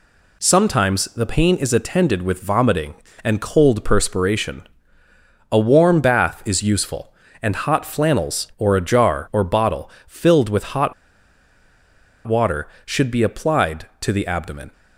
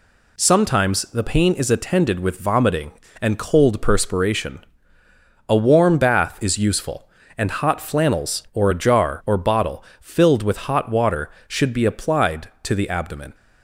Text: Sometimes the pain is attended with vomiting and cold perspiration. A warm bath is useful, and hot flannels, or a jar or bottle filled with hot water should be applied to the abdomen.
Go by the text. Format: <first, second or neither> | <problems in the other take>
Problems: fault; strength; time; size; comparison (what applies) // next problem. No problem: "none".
second | pauses between "bottle" and "filled"; slight; at 9.9 s; 0.16 s long; slight in the second // pauses between "hot" and "water"; strong; at 10.9 s; 1.3 s long